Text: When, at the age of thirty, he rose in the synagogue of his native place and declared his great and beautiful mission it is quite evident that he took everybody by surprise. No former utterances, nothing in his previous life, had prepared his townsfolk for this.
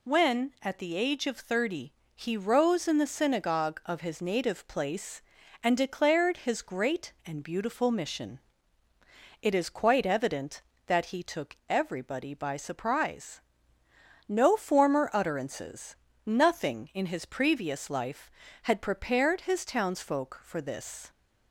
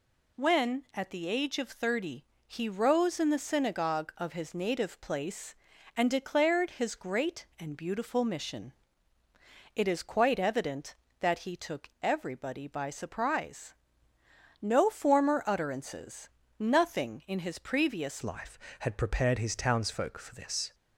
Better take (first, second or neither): first